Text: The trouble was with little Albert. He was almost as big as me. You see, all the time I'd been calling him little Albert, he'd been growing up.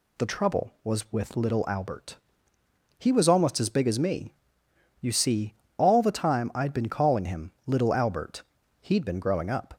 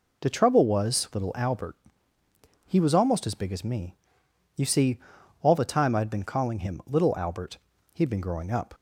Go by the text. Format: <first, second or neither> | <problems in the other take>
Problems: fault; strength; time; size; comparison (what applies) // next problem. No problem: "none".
first | skips "with"; at 1.1 s